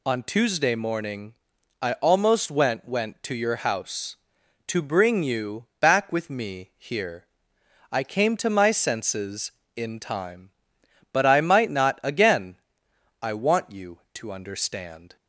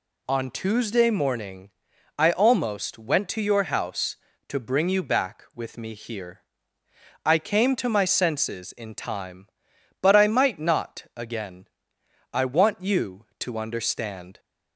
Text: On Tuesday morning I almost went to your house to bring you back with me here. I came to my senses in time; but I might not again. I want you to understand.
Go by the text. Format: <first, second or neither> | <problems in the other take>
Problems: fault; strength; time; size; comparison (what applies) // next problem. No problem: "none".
second | pauses between "morning" and "I"; noticeable; at 1.3 s; 0.48 s long; noticeable in the second // says "went" twice; at 2.8 s // pauses between "you" and "back"; slight; at 5.6 s; 0.16 s long